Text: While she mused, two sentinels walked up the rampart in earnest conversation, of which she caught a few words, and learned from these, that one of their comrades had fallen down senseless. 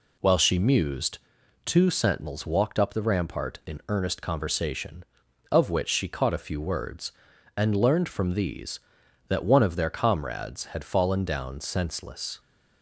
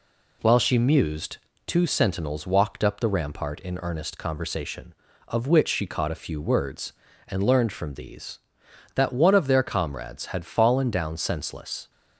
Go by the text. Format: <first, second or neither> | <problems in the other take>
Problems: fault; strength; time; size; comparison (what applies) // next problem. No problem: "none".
neither | none